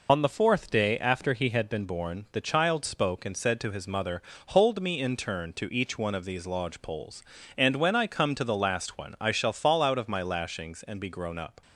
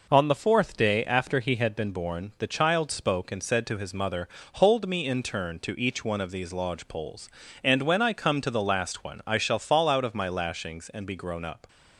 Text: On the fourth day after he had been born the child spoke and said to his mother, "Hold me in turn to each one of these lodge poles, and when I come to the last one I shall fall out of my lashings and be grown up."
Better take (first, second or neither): second